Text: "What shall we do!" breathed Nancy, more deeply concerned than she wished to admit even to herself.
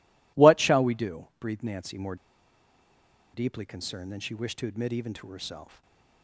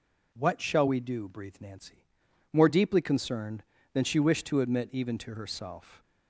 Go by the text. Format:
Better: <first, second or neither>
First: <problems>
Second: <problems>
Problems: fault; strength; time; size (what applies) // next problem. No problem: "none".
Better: second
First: pauses between "more" and "deeply"; at 2.1 s; 1.1 s long // stays silent after the last word; slight; from 5.6 s on; 0.6 s long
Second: none